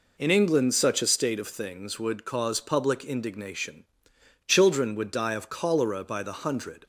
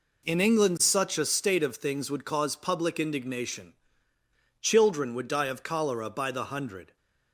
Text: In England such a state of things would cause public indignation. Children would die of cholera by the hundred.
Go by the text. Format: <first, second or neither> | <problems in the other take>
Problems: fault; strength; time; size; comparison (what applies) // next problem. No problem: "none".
neither | none